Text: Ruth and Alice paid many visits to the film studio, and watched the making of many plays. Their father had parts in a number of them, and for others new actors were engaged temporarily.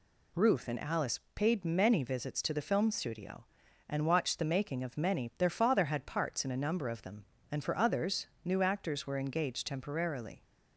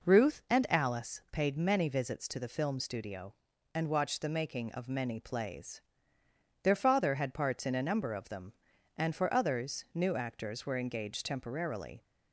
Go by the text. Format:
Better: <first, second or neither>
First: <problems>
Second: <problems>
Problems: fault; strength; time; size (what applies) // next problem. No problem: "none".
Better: second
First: pauses between "Alice" and "paid"; slight; at 1.1 s; 0.16 s long // skips "plays"; at 5.3 s // pauses between "others" and "new"; slight; at 8.2 s; 0.18 s long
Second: none